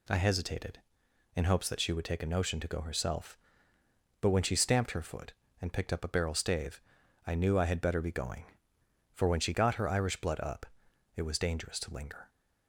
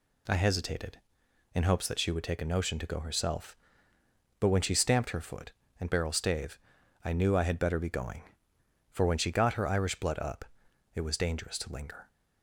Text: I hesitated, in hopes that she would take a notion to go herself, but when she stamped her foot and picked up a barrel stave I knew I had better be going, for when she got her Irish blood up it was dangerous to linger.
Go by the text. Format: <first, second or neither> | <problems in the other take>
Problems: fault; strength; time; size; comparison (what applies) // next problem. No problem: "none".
first | skips "picked up a"; at 5.9 s // pauses between "stave" and "I"; noticeable; at 6.5 s; 0.46 s long; noticeable in the first // pauses between "up" and "it"; noticeable; at 10.4 s; 0.52 s long; noticeable in the first